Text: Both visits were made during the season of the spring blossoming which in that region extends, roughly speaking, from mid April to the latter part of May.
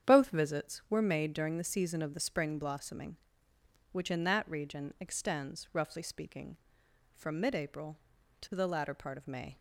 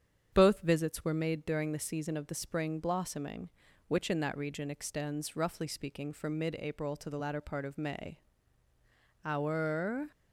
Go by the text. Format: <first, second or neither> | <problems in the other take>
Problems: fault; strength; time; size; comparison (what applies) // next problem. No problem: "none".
first | starts louder than the rest; strong; until 1.3 s; 8 dB; strong in the first // goes on to say "Our"; noticeable; from 9.2 s on; 0.86 s long